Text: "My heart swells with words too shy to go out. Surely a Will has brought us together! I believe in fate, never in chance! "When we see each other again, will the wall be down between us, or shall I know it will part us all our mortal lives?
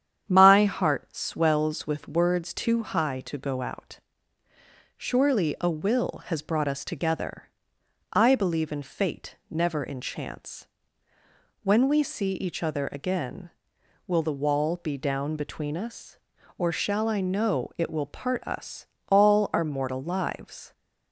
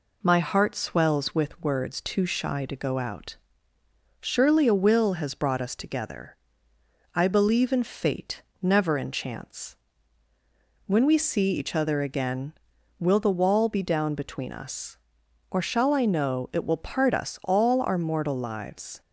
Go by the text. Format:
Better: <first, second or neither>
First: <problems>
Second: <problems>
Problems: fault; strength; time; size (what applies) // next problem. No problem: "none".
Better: second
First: starts louder than the rest; strong; until 1.2 s; 9 dB // says "high" for "shy"; at 2.8 s // pauses between "us" and "all"; slight; at 18.8 s; 0.22 s long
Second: none